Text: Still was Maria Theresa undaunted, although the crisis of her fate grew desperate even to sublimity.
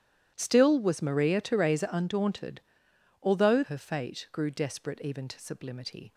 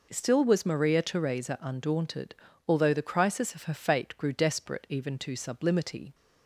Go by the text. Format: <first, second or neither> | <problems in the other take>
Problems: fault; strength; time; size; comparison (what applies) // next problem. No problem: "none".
second | starts louder than the rest; strong; until 1.3 s; 12 dB // skips "the crisis of"; at 3.6 s